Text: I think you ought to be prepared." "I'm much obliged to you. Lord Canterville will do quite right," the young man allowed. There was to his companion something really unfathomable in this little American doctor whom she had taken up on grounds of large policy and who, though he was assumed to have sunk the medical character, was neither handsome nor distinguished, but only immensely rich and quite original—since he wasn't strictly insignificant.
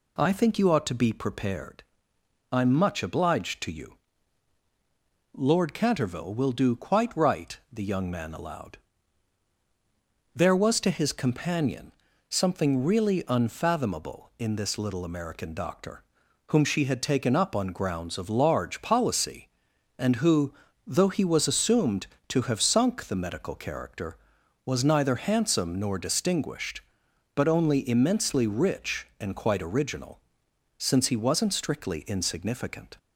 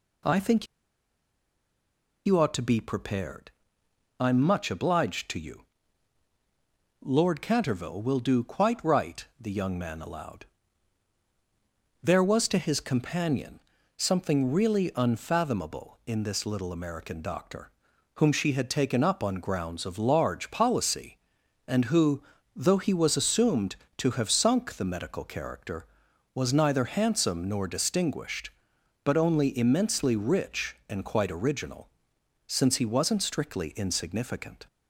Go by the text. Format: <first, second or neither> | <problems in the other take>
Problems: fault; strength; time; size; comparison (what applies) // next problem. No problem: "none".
first | pauses between "think" and "you"; strong; at 0.6 s; 1.5 s long // pauses between "companion" and "something"; at 13.5 s; 0.38 s long; also in the first // pauses between "doctor" and "whom"; at 17.6 s; 0.44 s long; also in the first